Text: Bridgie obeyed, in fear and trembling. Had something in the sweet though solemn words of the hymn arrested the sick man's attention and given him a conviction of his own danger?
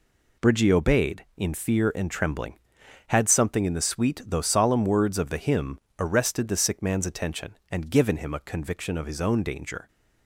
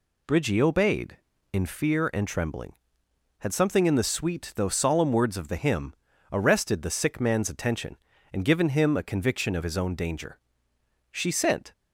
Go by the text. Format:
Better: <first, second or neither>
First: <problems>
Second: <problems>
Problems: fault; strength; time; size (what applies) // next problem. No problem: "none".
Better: first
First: pauses between "hymn" and "arrested"; slight; at 5.7 s; 0.20 s long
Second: pauses between "hymn" and "arrested"; at 5.9 s; 0.38 s long // goes on to say "She sent"; noticeable; from 11.0 s on; 0.62 s long